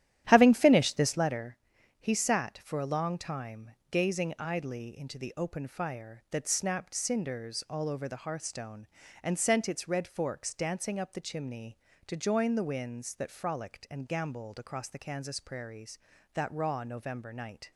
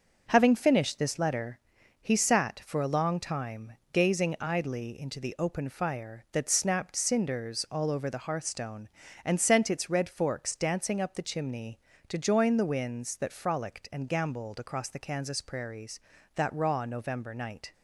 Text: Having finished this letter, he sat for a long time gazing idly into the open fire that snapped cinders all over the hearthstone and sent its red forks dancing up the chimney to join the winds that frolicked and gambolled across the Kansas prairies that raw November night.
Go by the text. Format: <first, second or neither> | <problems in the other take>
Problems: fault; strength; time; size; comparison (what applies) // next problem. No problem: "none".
second | starts louder than the rest; strong; until 1.4 s; 11.5 dB // pauses between "time" and "gazing"; slight; at 3.6 s; 0.22 s long; slight in the second